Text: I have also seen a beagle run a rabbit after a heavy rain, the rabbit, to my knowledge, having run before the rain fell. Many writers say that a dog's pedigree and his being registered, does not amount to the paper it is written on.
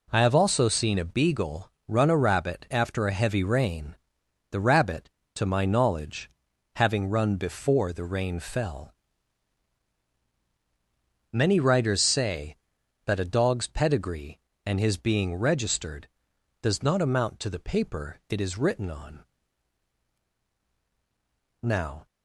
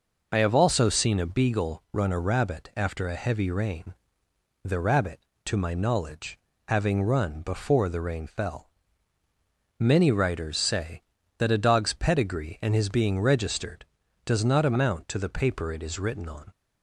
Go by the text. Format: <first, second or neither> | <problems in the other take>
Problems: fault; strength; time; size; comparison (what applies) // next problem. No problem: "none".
second | pauses between "beagle" and "run"; slight; at 1.7 s; 0.16 s long // goes on to say "Now"; slight; from 21.6 s on; 0.42 s long